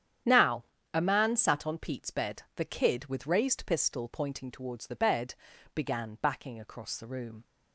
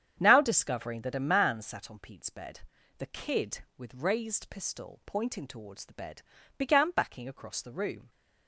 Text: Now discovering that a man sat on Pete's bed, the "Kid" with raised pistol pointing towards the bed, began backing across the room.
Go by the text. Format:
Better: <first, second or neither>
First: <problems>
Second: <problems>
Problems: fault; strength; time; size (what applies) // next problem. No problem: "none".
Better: second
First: starts louder than the rest; strong; until 1.5 s; 9.5 dB // skips "discovering that"; at 0.7 s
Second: starts louder than the rest; strong; until 1.2 s; 8 dB